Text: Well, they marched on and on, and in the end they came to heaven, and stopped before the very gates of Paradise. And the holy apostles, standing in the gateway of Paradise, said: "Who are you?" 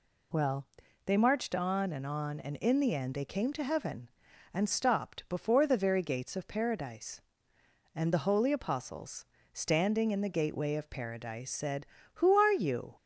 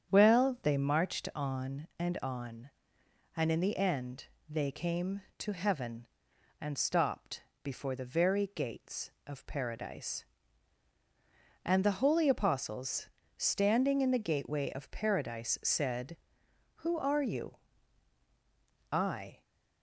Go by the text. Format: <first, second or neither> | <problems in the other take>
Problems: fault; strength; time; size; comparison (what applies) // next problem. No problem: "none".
first | starts louder than the rest; strong; until 1.1 s; 8 dB // pauses between "end" and "they"; slight; at 4.2 s; 0.24 s long // pauses between "stopped" and "before"; slight; at 7.4 s; 0.20 s long // goes on to say "I"; from 18.9 s on; 0.50 s long